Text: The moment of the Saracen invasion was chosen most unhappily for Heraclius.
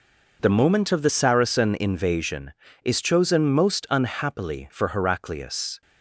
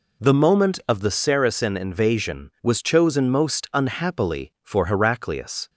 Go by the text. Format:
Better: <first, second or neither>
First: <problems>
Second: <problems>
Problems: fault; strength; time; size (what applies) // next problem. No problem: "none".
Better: second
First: says "is" for "was"; at 2.8 s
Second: none